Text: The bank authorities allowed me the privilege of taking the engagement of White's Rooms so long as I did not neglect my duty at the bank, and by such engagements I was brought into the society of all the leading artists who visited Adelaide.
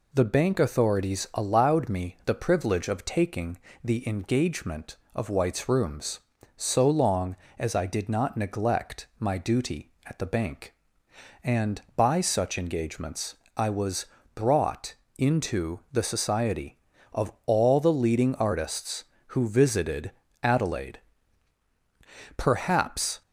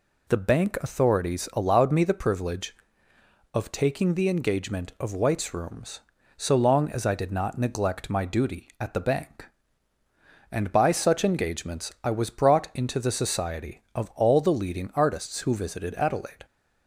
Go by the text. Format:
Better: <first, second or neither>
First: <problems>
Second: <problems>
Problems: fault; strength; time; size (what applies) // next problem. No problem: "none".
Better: second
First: pauses between "taking" and "the"; slight; at 3.5 s; 0.24 s long // pauses between "engagements" and "I"; slight; at 13.3 s; 0.20 s long // pauses between "was" and "brought"; slight; at 14.0 s; 0.30 s long // pauses between "brought" and "into"; slight; at 14.9 s; 0.22 s long // pauses between "visited" and "Adelaide"; slight; at 20.1 s; 0.32 s long // goes on to say "Perhaps"; noticeable; from 22.3 s on; 0.86 s long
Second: none